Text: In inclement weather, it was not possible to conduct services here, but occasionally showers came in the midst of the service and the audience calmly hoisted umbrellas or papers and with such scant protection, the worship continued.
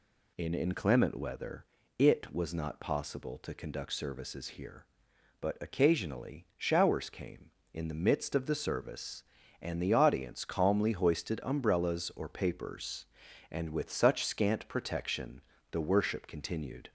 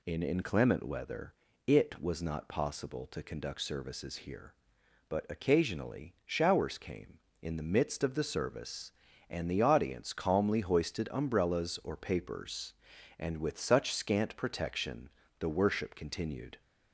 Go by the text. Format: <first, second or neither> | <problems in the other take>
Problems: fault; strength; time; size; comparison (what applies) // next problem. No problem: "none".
neither | none